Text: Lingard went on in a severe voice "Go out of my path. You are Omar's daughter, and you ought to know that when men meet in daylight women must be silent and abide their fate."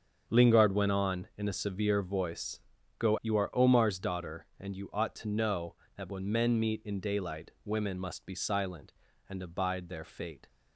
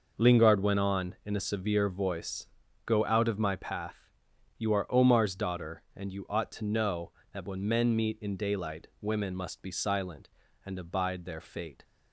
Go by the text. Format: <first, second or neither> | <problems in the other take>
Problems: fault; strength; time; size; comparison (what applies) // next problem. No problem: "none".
second | starts louder than the rest; until 1.2 s; 7 dB // pauses between "voice" and "Go"; at 2.5 s; 0.40 s long; also in the second // skips "out of my path"; at 3.1 s // pauses between "daylight" and "women"; slight; at 7.4 s; 0.16 s long; slight in the second